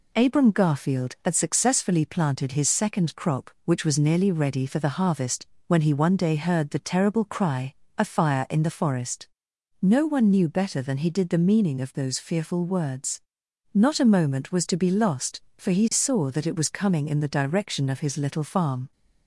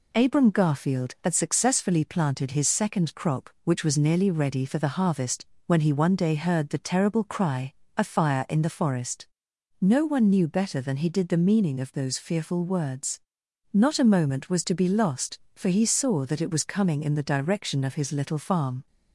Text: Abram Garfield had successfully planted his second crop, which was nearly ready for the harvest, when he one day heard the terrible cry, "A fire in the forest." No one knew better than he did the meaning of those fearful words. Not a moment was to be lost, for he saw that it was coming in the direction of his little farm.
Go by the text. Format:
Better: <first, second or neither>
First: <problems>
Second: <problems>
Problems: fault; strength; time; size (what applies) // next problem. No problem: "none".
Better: neither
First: none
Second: none